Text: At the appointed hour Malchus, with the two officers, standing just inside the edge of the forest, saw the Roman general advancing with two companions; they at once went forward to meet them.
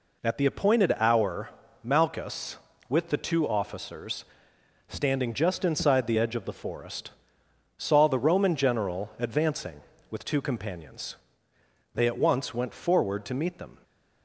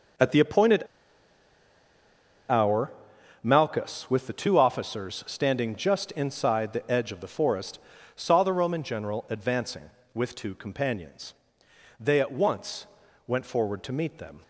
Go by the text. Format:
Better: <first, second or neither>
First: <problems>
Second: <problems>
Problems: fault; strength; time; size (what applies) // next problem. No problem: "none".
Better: first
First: pauses between "hour" and "Malchus"; slight; at 1.5 s; 0.34 s long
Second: pauses between "appointed" and "hour"; strong; at 0.8 s; 1.6 s long // pauses between "hour" and "Malchus"; noticeable; at 2.9 s; 0.48 s long // pauses between "once" and "went"; at 12.8 s; 0.42 s long